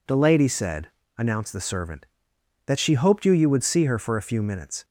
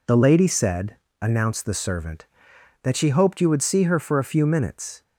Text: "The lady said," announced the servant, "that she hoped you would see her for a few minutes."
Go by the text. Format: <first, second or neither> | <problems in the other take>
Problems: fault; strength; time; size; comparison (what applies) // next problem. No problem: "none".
second | says "you" twice; at 3.3 s